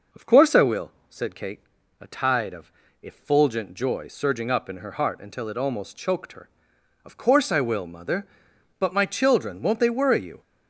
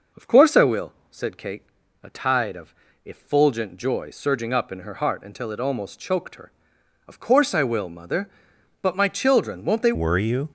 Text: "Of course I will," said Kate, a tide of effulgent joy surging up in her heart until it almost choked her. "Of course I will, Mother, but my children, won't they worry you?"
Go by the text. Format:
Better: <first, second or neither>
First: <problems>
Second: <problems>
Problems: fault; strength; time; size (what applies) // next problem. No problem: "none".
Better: first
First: pauses between "of" and "effulgent"; slight; at 2.7 s; 0.28 s long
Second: pauses between "of" and "effulgent"; slight; at 2.7 s; 0.28 s long // changes voice at "worry"; from 9.9 s on; 0.5 s long